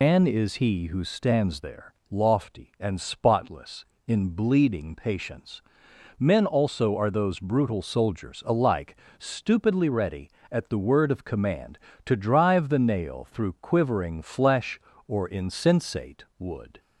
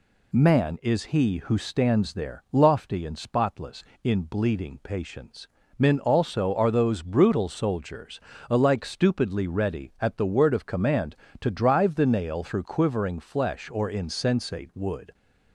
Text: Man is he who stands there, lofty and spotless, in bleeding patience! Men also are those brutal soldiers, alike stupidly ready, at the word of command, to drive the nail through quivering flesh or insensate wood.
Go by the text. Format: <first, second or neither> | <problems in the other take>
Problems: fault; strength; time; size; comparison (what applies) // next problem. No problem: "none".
second | loses the start of "Man"; at 0.0 s; 145 ms // pauses between "alike" and "stupidly"; slight; at 8.9 s; 0.22 s long // pauses between "insensate" and "wood"; slight; at 16.2 s; 0.16 s long